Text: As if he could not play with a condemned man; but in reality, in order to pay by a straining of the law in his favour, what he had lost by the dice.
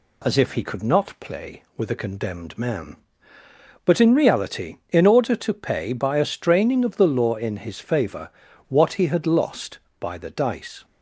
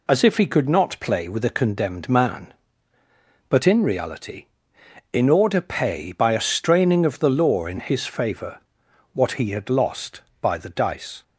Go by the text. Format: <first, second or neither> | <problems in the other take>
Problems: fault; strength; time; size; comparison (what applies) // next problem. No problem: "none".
first | skips "to"; at 5.6 s